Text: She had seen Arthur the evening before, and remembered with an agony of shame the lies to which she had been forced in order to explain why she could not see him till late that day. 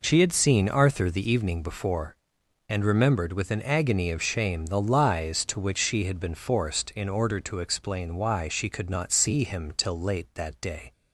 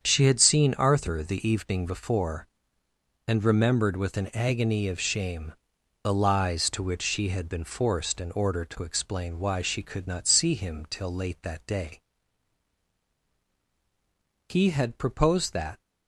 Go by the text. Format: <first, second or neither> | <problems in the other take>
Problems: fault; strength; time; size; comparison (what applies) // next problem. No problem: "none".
first | starts louder than the rest; strong; until 1.0 s; 7.5 dB // pauses between "shame" and "the"; noticeable; at 5.5 s; 0.50 s long // goes on to say "He had proposed that"; from 14.4 s on; 1.3 s long